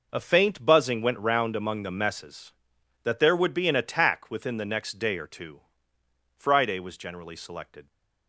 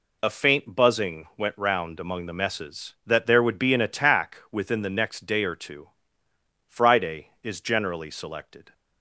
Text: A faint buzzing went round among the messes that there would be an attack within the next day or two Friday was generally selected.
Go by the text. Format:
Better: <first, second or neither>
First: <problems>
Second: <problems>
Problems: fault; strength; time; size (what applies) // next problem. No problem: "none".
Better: first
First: pauses between "two" and "Friday"; noticeable; at 5.6 s; 0.78 s long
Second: pauses between "two" and "Friday"; noticeable; at 5.8 s; 0.78 s long // says "is" for "was"; at 7.4 s